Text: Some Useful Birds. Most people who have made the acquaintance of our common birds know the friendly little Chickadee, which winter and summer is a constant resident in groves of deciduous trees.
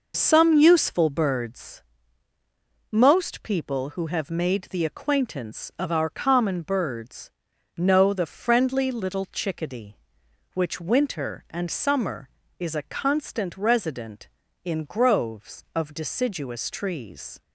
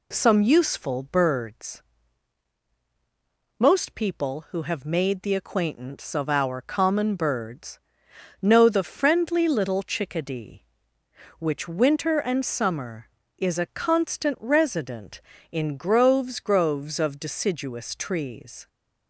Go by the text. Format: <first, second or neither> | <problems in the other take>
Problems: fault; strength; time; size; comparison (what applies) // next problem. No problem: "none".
first | pauses between "birds" and "know"; noticeable; at 7.7 s; 0.62 s long; noticeable in the first // says "groves" twice; at 16.3 s